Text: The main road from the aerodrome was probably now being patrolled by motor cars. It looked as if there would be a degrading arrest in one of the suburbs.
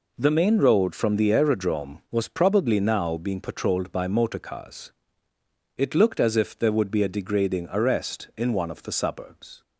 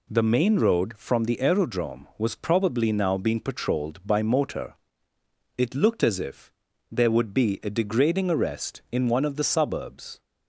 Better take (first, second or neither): first